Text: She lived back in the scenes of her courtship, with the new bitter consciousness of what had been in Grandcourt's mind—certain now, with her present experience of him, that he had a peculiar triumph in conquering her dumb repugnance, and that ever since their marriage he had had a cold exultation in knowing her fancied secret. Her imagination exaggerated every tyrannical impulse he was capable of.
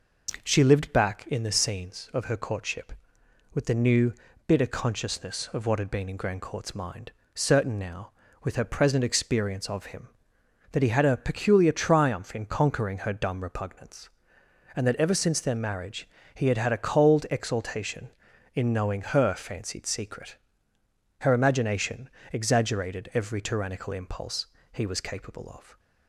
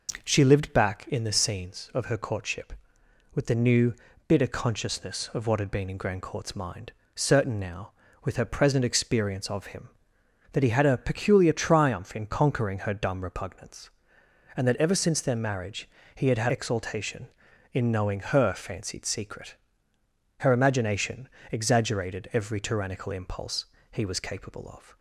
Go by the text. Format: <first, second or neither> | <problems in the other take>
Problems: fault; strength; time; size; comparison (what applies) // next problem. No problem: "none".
first | pauses between "new" and "bitter"; slight; at 3.9 s; 0.34 s long; slight in the first // pauses between "marriage" and "he"; slight; at 15.8 s; 0.28 s long; slight in the first // skips "a cold"; at 16.4 s // pauses between "imagination" and "exaggerated"; slight; at 21.2 s; 0.24 s long; slight in the first // pauses between "impulse" and "he"; slight; at 23.6 s; 0.26 s long; slight in the first